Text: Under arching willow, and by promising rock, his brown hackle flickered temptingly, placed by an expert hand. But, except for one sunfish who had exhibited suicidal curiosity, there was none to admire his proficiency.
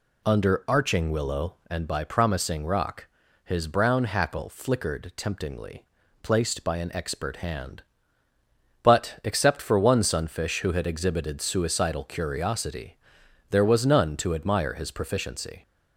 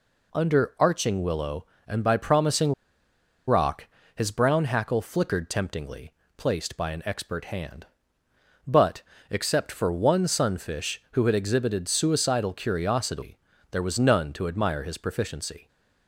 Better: first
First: none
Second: pauses between "promising" and "rock"; noticeable; at 2.7 s; 0.75 s long

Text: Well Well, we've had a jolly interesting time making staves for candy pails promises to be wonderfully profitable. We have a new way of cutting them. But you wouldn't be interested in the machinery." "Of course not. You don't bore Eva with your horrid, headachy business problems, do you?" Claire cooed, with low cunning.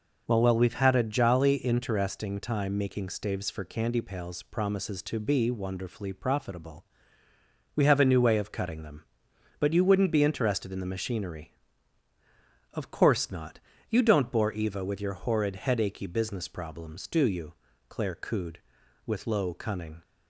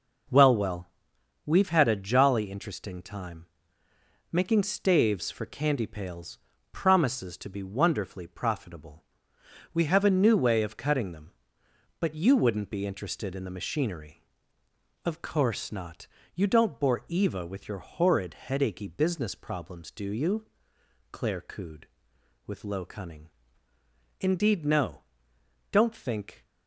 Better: first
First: none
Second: pauses between "time" and "making"; noticeable; at 3.4 s; 0.84 s long // pauses between "pails" and "promises"; slight; at 6.3 s; 0.34 s long // goes on to say "Indeed no Don't think"; strong; from 24.2 s on; 2.2 s long

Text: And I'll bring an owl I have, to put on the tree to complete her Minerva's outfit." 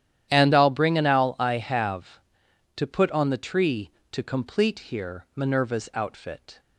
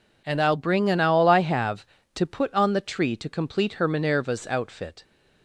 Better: second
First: starts louder than the rest; strong; until 1.3 s; 11 dB // says "here" for "her"; at 4.7 s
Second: none

